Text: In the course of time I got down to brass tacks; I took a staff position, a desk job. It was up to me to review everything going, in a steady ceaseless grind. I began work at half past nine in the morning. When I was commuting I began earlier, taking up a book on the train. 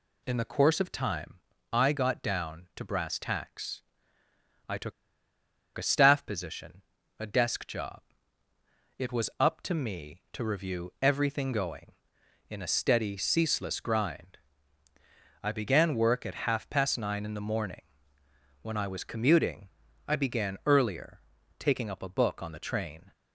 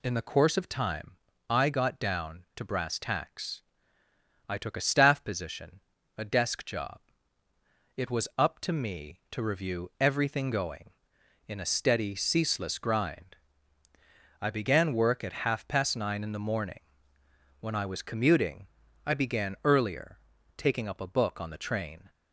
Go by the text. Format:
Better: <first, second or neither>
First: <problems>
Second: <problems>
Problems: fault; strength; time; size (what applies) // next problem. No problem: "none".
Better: second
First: pauses between "time" and "I"; slight; at 1.3 s; 0.34 s long // pauses between "took" and "a"; noticeable; at 4.9 s; 0.84 s long // pauses between "commuting" and "I"; at 19.6 s; 0.38 s long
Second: pauses between "time" and "I"; slight; at 1.1 s; 0.34 s long // pauses between "commuting" and "I"; at 18.6 s; 0.38 s long